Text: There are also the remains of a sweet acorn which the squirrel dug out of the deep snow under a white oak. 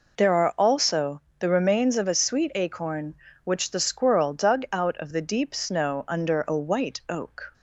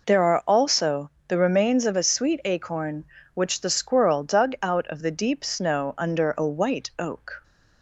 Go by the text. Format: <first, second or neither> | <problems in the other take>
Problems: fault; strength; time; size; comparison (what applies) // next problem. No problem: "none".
neither | pauses between "also" and "the"; slight; the same in both